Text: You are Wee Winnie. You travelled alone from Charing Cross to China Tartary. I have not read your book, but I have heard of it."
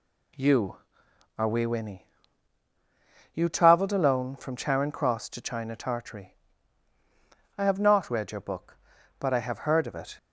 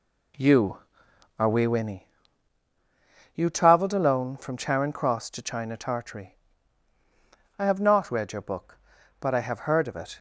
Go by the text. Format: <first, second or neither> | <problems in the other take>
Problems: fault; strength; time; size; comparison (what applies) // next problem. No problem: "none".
first | starts louder than the rest; slight; until 2.0 s; 2 dB